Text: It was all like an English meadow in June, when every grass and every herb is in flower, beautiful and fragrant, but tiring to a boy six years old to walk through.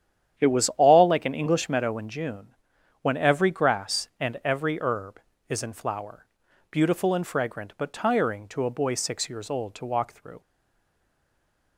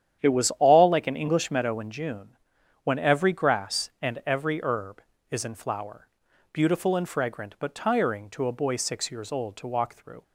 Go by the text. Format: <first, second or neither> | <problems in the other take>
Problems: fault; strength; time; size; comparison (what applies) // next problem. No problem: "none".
second | starts louder than the rest; strong; until 1.4 s; 9.5 dB; strong in the second // stays silent after the last word; noticeable; from 10.4 s on; 1.3 s long